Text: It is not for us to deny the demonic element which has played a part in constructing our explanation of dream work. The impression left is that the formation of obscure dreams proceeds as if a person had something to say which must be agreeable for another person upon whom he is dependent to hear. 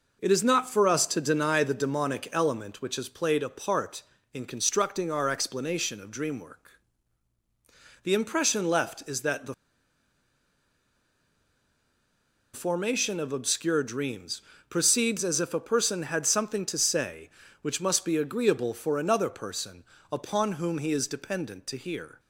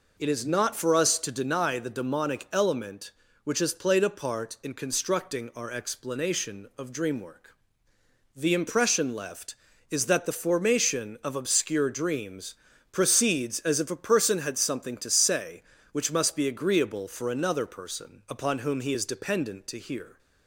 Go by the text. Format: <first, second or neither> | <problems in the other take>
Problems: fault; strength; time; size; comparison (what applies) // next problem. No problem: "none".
second | pauses between "the" and "formation"; strong; at 9.5 s; 2.9 s long // pauses between "dreams" and "proceeds"; slight; at 14.4 s; 0.28 s long; slight in the second // pauses between "person" and "upon"; slight; at 19.8 s; 0.30 s long